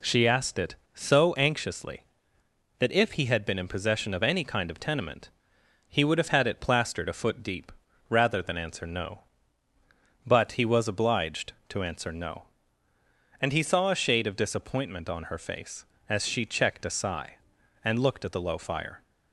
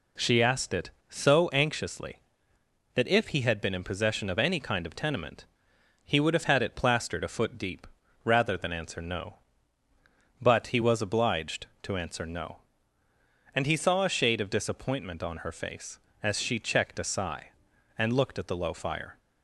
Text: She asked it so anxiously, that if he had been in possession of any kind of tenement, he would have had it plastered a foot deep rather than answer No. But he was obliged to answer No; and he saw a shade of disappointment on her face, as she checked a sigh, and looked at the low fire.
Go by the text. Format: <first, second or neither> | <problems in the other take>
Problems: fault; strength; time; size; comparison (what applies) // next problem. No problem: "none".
neither | pauses between "deep" and "rather"; the same in both